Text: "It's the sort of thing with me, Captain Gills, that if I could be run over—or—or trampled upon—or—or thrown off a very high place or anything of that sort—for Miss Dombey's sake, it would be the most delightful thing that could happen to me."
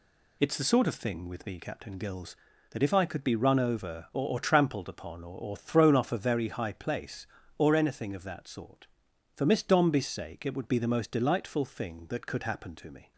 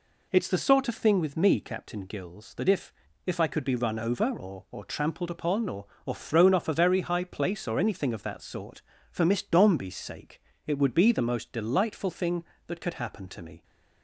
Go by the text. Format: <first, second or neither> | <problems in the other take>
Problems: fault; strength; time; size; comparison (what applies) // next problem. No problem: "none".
first | says "if" twice; at 3.2 s